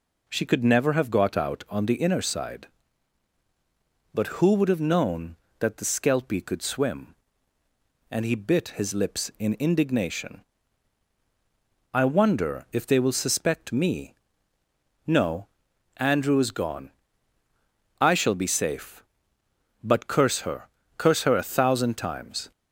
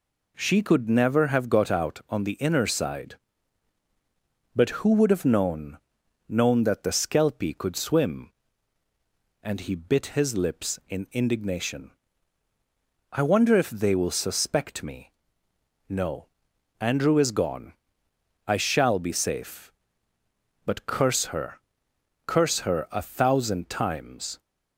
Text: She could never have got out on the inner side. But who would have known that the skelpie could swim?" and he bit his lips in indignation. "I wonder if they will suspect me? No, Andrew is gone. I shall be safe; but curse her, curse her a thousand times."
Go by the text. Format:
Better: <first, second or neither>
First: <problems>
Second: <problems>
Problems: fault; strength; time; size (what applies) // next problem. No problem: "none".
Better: first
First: none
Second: says "known" twice; at 6.2 s